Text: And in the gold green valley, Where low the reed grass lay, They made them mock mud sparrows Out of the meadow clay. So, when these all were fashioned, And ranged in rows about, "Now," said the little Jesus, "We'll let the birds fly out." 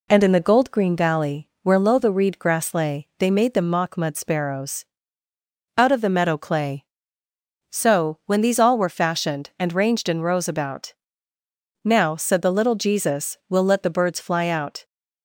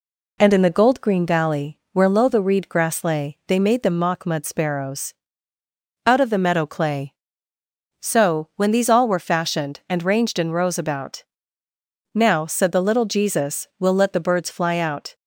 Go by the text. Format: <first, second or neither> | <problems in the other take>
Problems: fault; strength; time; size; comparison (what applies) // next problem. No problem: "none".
neither | pauses between "sparrows" and "Out"; noticeable; the same in both